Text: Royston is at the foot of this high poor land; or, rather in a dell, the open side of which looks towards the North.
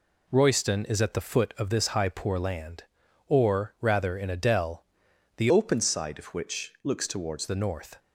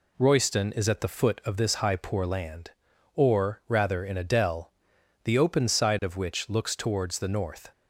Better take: second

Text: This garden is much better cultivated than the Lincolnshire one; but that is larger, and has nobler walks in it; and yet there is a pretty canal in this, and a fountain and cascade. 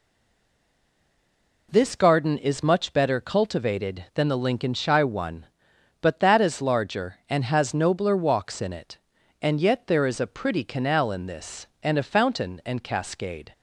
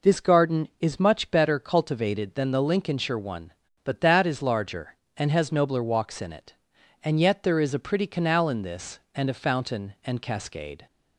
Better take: second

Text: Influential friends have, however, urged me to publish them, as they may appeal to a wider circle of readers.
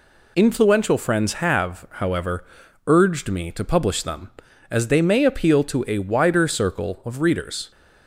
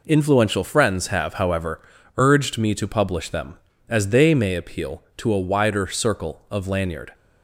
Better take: first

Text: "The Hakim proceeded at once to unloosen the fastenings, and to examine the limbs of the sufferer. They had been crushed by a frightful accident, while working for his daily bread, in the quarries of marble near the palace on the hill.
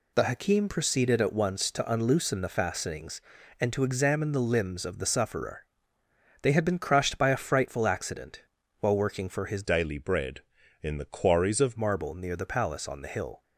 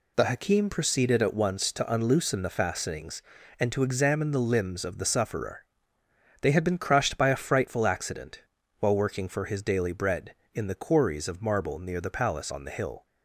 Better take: second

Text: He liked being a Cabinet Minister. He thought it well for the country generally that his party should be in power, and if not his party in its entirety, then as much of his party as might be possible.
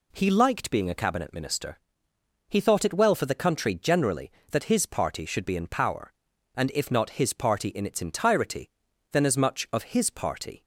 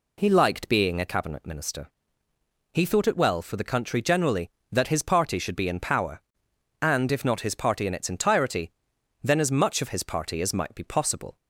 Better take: second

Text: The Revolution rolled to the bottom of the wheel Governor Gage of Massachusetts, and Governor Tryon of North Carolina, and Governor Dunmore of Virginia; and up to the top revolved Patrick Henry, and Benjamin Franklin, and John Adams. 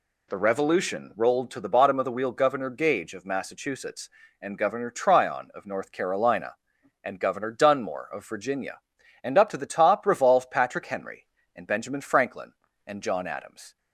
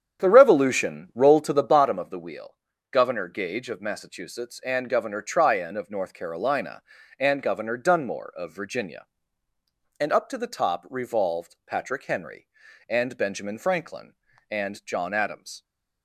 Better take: first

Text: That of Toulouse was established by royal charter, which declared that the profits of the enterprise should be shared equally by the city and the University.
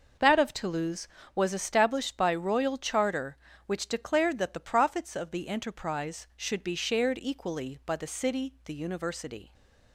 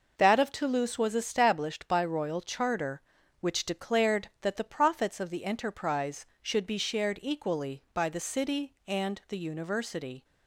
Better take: second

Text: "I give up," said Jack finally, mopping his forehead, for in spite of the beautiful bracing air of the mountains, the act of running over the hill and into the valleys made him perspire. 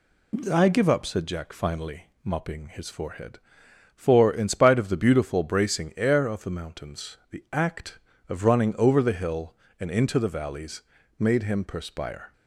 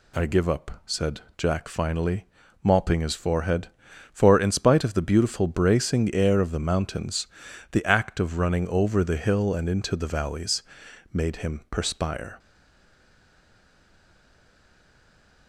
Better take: first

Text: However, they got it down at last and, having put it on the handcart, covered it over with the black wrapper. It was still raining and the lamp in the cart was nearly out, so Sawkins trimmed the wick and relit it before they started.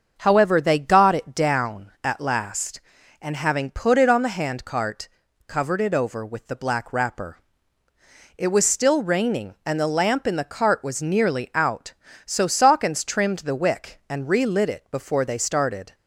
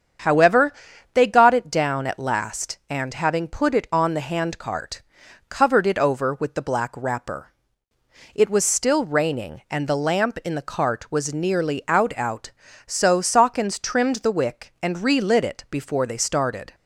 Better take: first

